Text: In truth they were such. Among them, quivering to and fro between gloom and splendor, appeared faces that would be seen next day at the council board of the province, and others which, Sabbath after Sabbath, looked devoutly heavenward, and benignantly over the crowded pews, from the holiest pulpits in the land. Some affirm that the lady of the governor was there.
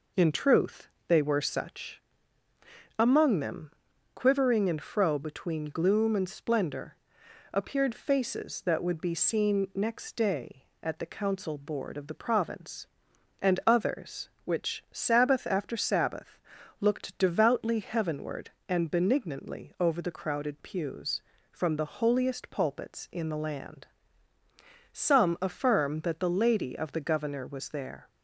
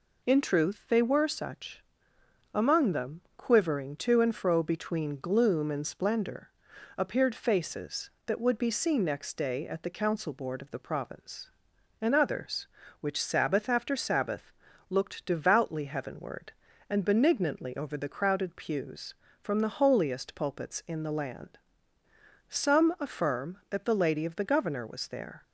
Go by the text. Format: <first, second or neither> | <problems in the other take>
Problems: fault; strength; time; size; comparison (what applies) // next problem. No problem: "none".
second | pauses between "truth" and "they"; slight; at 0.8 s; 0.20 s long // skips "to"; at 4.6 s